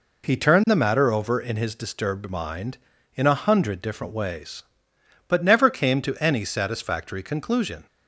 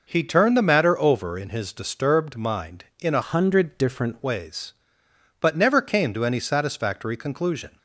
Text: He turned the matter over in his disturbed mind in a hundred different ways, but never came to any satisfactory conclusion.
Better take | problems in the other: first | changes voice from "hundred" to "different"; from 3.2 to 4.2 s; 1.0 s long

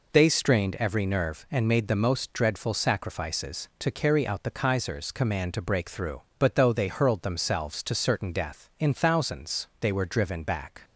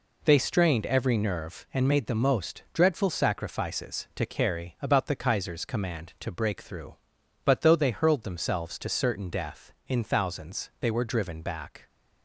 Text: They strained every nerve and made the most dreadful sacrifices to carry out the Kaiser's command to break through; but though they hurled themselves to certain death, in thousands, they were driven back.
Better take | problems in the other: first | says "about" for "out"; at 4.8 s

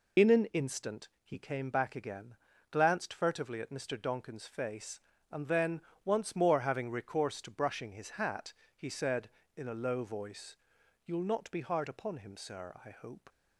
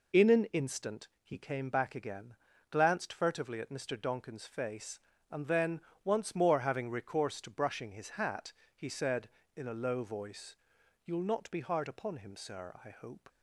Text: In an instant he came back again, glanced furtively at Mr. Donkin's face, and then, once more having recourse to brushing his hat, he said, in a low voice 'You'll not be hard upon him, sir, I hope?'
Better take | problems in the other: second | loses the start of "In"; at 0.1 s; 30 ms // pauses between "voice" and "You'll"; noticeable; at 10.5 s; 0.48 s long; noticeable in the second

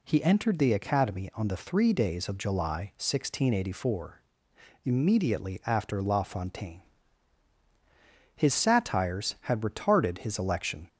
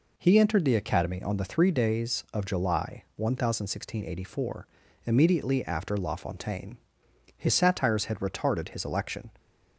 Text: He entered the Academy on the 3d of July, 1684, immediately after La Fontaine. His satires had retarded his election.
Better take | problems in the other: neither | none

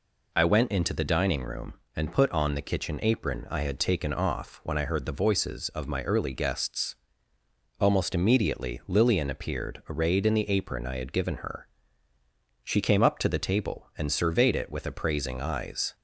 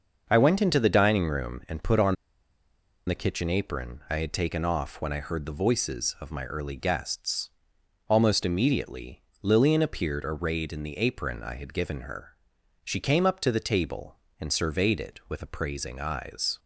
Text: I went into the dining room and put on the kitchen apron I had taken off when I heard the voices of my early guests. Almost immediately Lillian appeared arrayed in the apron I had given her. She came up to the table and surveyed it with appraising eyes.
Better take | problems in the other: first | starts louder than the rest; until 1.2 s; 6 dB // pauses between "on" and "the"; noticeable; at 2.1 s; 0.91 s long // pauses between "immediately" and "Lillian"; slight; at 9.2 s; 0.18 s long

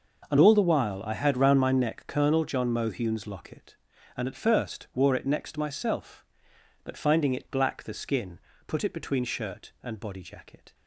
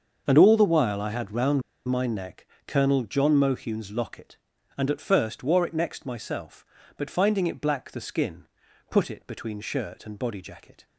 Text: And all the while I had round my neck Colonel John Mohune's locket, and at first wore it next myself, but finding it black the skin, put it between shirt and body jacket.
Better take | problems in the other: first | starts louder than the rest; until 1.2 s; 6.5 dB // pauses between "round" and "my"; slight; at 1.6 s; 0.24 s long // pauses between "neck" and "Colonel"; slight; at 2.4 s; 0.20 s long

